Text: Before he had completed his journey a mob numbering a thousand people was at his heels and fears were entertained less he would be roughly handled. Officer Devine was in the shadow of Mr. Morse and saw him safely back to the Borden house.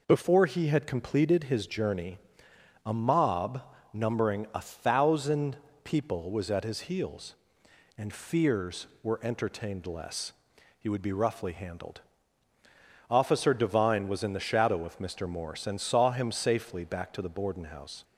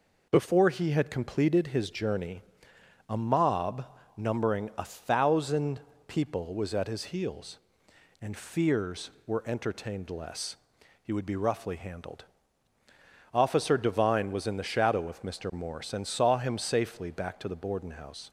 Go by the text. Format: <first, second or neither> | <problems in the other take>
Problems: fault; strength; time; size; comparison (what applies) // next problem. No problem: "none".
neither | pauses between "journey" and "a"; noticeable; the same in both // pauses between "mob" and "numbering"; slight; the same in both // pauses between "thousand" and "people"; slight; the same in both // pauses between "less" and "he"; noticeable; the same in both